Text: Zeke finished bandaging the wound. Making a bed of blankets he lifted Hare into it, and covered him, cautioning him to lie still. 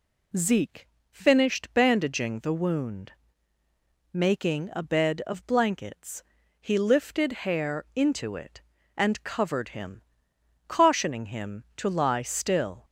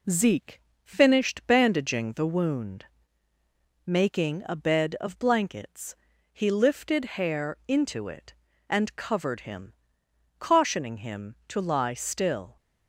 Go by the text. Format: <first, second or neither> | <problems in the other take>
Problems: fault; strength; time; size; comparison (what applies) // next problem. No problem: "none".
first | gets quieter; slight; throughout; 2.5 dB // pauses between "Zeke" and "finished"; slight; at 0.6 s; 0.22 s long; slight in the first // pauses between "blankets" and "he"; at 5.9 s; 0.38 s long; also in the first